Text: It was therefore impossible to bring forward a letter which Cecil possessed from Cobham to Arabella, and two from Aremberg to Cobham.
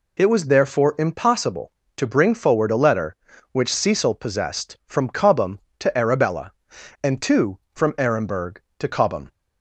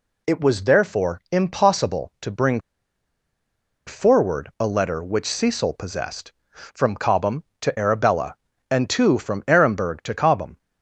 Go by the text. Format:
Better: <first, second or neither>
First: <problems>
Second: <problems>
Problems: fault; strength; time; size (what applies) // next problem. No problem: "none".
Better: first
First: none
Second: pauses between "bring" and "forward"; strong; at 2.5 s; 1.2 s long